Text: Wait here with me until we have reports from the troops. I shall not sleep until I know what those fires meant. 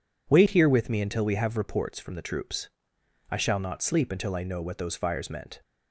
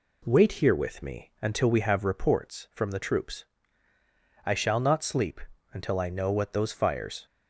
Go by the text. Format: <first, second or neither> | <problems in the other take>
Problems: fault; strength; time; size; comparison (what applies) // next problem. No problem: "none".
first | pauses between "sleep" and "until"; slight; at 5.4 s; 0.32 s long // stops before "meant"; at 7.2 s